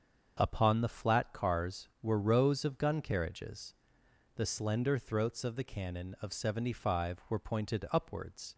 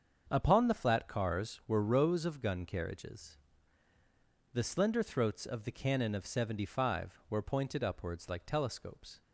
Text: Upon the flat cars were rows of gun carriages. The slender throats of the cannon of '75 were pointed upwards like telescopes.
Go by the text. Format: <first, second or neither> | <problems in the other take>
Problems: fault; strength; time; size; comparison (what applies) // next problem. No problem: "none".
second | starts louder than the rest; until 1.4 s; 7 dB; also in the second // stops before "like telescopes"; at 8.5 s